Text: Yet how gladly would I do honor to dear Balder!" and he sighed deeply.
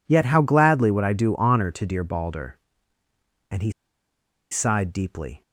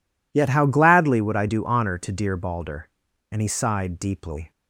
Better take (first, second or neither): second